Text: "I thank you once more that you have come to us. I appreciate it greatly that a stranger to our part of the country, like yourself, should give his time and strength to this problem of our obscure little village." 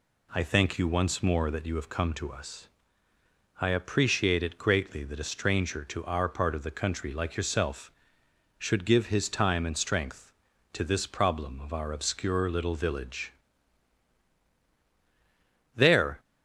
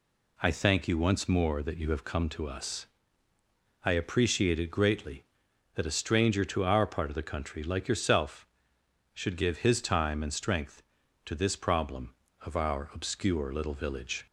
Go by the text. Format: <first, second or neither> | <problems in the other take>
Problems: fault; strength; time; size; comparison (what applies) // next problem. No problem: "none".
second | goes on to say "There"; slight; from 15.7 s on; 0.44 s long